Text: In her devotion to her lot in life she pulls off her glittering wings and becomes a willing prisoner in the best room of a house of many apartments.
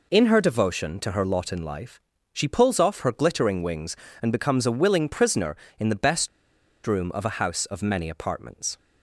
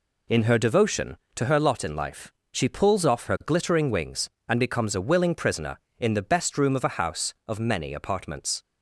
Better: second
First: pauses between "life" and "she"; slight; at 1.9 s; 0.32 s long // pauses between "best" and "room"; noticeable; at 6.2 s; 0.57 s long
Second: pauses between "life" and "she"; slight; at 2.3 s; 0.18 s long

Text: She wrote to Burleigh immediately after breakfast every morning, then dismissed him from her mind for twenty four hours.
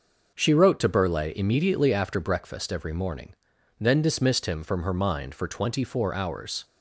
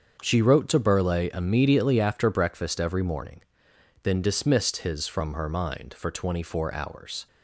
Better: first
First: none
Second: starts louder than the rest; until 1.2 s; 7 dB // says "his" for "him"; at 4.7 s

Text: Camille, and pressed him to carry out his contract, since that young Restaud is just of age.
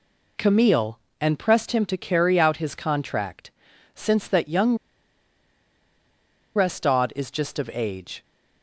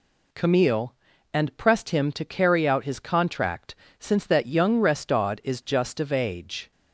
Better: second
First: pauses between "young" and "Restaud"; strong; at 4.7 s; 1.7 s long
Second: none

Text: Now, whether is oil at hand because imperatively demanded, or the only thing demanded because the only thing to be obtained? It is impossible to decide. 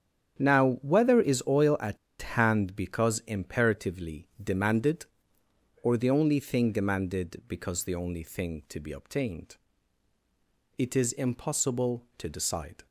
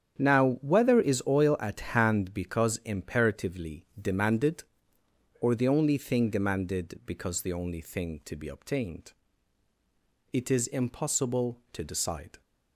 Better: second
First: starts louder than the rest; strong; until 1.4 s; 8.5 dB // pauses between "at" and "hand"; slight; at 1.9 s; 0.24 s long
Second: starts louder than the rest; strong; until 1.2 s; 8.5 dB

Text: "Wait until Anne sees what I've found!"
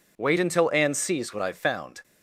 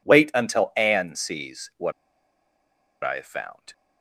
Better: first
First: none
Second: pauses between "what" and "I've"; at 1.9 s; 1.1 s long

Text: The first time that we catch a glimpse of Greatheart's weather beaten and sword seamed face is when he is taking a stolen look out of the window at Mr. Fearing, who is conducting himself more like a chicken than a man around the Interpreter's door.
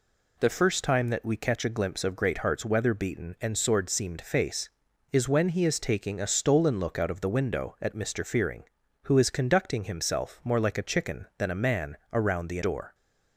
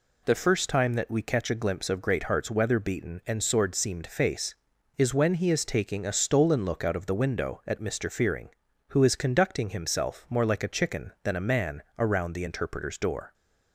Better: second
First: pauses between "man" and "around"; slight; at 11.9 s; 0.16 s long // skips "Interpreter's"; at 12.6 s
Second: pauses between "man" and "around"; slight; at 11.8 s; 0.16 s long

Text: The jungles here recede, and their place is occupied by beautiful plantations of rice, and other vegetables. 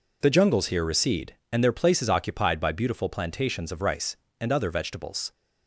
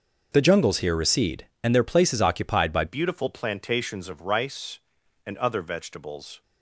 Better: first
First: none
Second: starts louder than the rest; until 1.3 s; 6.5 dB // changes voice at "beautiful"; from 2.8 s on; 3.6 s long

